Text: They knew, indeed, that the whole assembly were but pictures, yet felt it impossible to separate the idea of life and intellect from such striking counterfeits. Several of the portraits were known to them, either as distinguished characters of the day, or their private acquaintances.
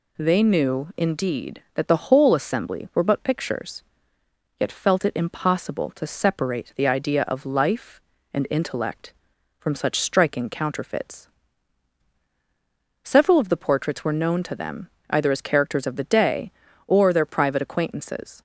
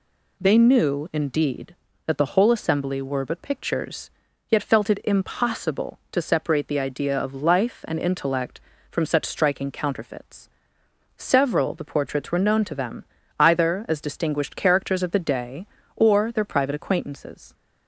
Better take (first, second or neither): second